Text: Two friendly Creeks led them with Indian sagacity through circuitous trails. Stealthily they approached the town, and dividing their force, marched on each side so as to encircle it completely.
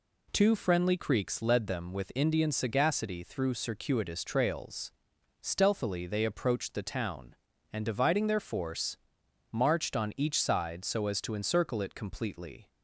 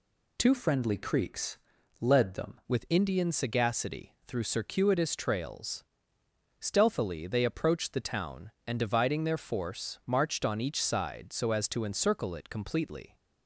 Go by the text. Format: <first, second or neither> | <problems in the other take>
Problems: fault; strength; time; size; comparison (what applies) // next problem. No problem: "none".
first | changes voice from "friendly" to "them"; from 0.5 to 2.6 s; 2.1 s long // pauses between "Creeks" and "led"; at 1.5 s; 0.44 s long